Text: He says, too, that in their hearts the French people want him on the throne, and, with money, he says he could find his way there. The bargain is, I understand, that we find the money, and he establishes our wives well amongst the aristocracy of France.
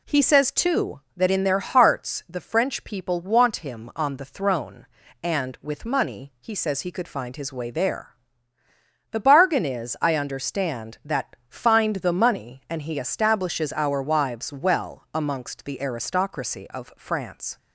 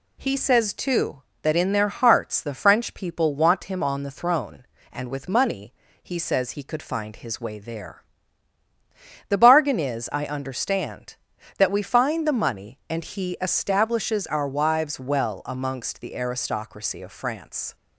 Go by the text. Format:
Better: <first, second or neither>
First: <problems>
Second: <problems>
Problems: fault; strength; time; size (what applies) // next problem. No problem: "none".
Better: second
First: skips "we"; at 11.4 s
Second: none